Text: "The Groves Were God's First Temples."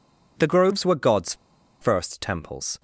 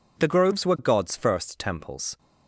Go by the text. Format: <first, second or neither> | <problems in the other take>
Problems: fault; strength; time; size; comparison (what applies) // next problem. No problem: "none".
second | pauses between "God's" and "First"; noticeable; at 1.3 s; 0.47 s long